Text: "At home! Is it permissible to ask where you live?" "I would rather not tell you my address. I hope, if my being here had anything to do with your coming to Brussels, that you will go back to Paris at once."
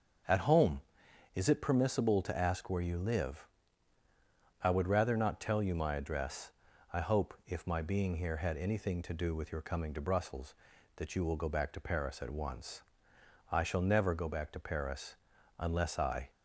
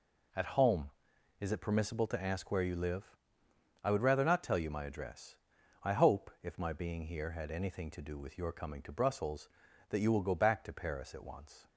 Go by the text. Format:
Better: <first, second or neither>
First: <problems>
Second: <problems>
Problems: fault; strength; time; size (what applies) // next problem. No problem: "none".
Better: second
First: starts louder than the rest; until 1.7 s; 6.5 dB // goes on to say "I shall never go back to Paris unless I"; strong; from 13.5 s on; 2.7 s long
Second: none